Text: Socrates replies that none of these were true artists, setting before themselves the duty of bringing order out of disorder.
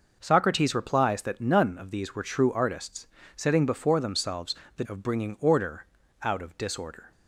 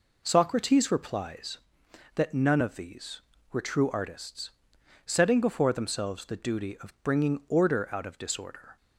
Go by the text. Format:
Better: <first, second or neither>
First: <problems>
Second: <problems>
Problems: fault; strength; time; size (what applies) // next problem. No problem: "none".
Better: second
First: pauses between "themselves" and "the"; slight; at 4.5 s; 0.22 s long // skips "duty"; at 4.8 s // pauses between "order" and "out"; at 5.8 s; 0.38 s long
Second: none